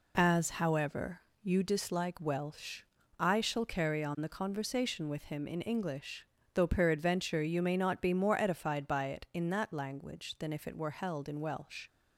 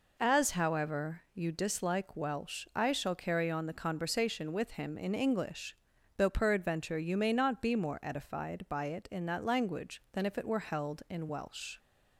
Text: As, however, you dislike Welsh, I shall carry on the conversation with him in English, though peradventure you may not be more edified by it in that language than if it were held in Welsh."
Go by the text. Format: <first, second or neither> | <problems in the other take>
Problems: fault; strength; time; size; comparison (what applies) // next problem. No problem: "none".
neither | none